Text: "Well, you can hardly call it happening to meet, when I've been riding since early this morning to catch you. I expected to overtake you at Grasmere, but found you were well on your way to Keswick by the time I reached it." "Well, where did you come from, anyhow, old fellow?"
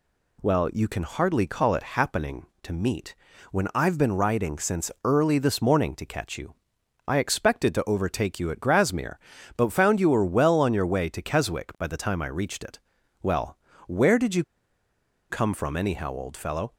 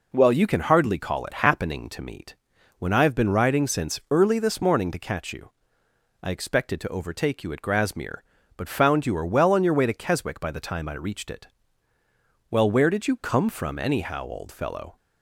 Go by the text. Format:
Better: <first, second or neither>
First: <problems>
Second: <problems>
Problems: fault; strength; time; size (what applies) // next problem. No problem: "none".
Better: second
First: pauses between "you" and "come"; noticeable; at 14.4 s; 0.86 s long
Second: none